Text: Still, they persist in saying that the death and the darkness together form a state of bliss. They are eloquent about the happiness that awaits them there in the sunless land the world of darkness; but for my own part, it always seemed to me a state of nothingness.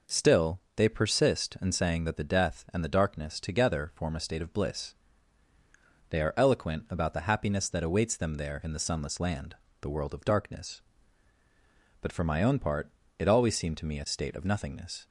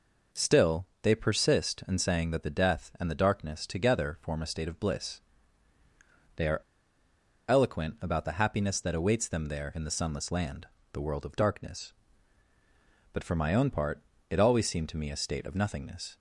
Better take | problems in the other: first | pauses between "are" and "eloquent"; noticeable; at 6.5 s; 0.89 s long // pauses between "land" and "the"; slight; at 10.6 s; 0.26 s long; slight in the first

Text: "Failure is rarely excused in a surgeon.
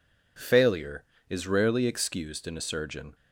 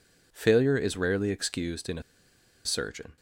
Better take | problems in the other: first | pauses between "a" and "surgeon"; noticeable; at 2.0 s; 0.64 s long

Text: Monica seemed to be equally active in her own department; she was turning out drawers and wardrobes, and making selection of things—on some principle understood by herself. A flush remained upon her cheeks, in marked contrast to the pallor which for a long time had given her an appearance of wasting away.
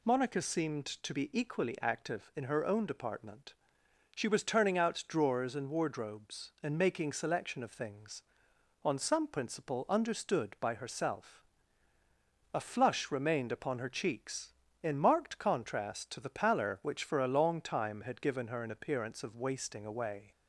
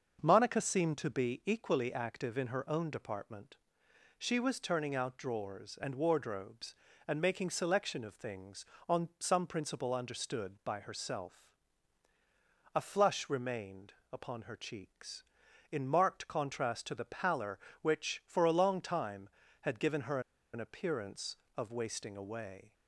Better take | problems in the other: first | starts louder than the rest; until 1.2 s; 6.5 dB // pauses between "remained" and "upon"; slight; at 13.9 s; 0.18 s long // pauses between "her" and "an"; slight; at 20.1 s; 0.33 s long

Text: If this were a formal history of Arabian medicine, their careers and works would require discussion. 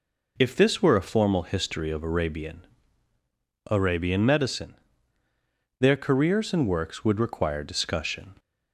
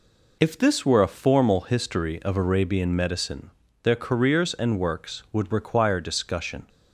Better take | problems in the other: second | says "Arabian" twice; at 3.7 s

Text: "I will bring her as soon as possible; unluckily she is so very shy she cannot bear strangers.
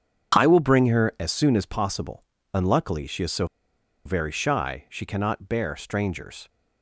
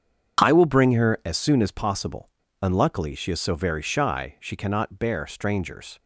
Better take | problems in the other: second | starts louder than the rest; strong; until 1.4 s; 7.5 dB; strong in the second // pauses between "so" and "very"; noticeable; at 3.4 s; 0.60 s long

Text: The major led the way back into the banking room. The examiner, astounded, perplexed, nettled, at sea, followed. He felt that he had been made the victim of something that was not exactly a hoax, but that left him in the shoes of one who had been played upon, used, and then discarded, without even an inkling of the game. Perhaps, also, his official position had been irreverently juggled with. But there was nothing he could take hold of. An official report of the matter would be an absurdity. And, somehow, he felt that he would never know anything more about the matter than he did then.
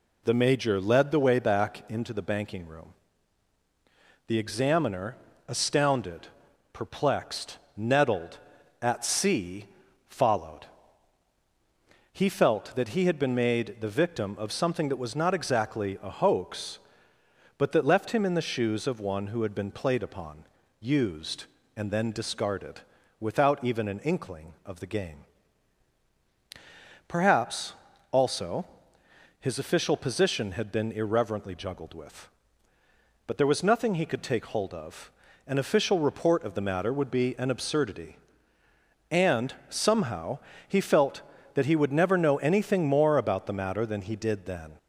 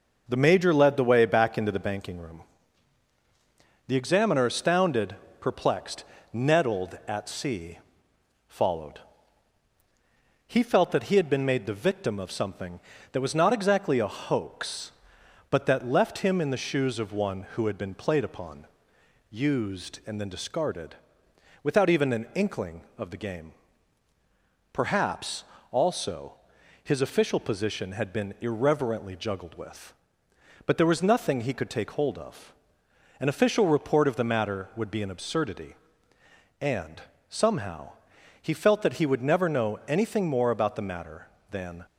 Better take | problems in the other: first | stops before "he did then"; at 41.8 s

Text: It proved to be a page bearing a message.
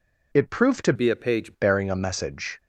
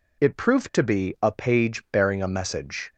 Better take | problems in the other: second | changes voice from "be" to "page"; from 0.9 to 1.5 s; 0.6 s long

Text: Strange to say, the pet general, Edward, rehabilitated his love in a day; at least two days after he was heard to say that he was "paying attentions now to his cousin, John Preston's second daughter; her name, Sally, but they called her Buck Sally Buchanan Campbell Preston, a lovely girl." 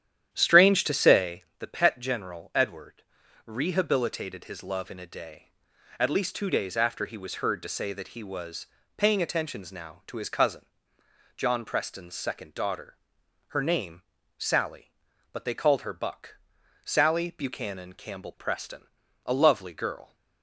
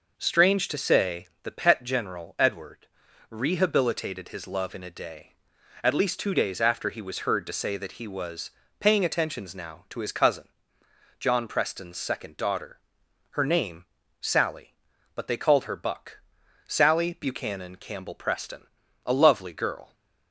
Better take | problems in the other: second | starts louder than the rest; strong; until 1.2 s; 10.5 dB // pauses between "was" and "paying"; slight; at 8.6 s; 0.30 s long; slight in the second // pauses between "Buck" and "Sally"; noticeable; at 16.3 s; 0.48 s long; noticeable in the second

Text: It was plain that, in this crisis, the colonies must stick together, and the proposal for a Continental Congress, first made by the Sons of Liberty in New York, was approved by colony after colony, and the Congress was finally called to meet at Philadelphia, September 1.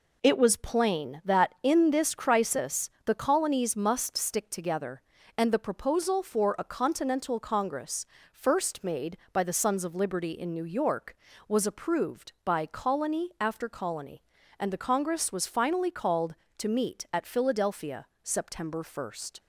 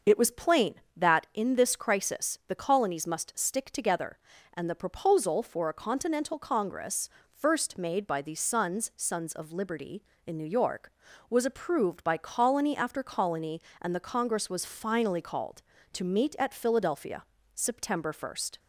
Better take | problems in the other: first | starts louder than the rest; until 1.2 s; 6 dB // says "Sons" twice; at 8.9 s

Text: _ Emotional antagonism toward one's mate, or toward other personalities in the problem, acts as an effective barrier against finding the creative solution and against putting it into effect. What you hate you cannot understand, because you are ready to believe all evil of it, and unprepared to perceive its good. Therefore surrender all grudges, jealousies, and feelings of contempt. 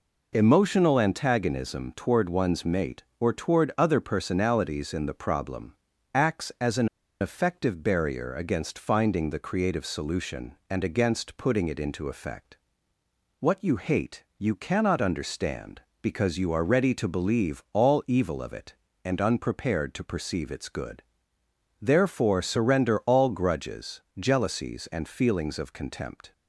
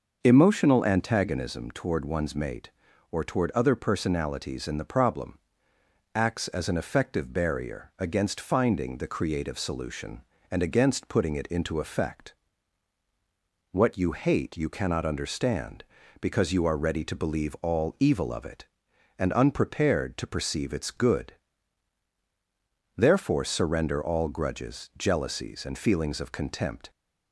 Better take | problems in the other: second | pauses between "an" and "effective"; slight; at 6.8 s; 0.33 s long

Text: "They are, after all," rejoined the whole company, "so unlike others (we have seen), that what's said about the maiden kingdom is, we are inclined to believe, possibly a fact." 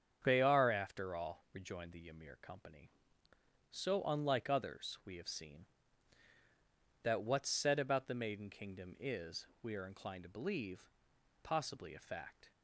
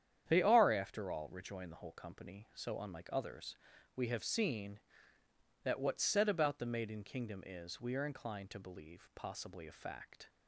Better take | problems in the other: second | starts louder than the rest; strong; until 1.2 s; 7.5 dB; strong in the second // says "ymir" for "whole"; at 2.0 s

